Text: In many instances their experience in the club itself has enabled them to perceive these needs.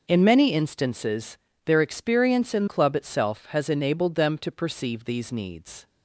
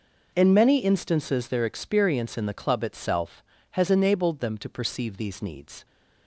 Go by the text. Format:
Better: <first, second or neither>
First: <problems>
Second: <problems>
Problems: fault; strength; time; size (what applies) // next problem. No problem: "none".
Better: second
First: pauses between "instances" and "their"; slight; at 1.3 s; 0.28 s long // skips "the"; at 2.6 s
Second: none